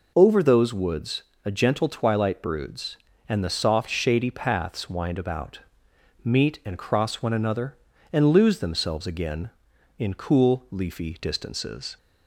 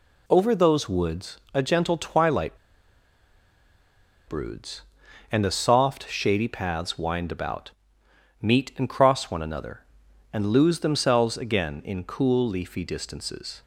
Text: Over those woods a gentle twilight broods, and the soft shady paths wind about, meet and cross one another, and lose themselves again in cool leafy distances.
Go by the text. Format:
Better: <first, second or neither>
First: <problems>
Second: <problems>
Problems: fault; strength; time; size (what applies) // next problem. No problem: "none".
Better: first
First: pauses between "woods" and "a"; slight; at 1.2 s; 0.22 s long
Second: pauses between "woods" and "a"; slight; at 1.3 s; 0.16 s long // pauses between "twilight" and "broods"; strong; at 2.5 s; 1.7 s long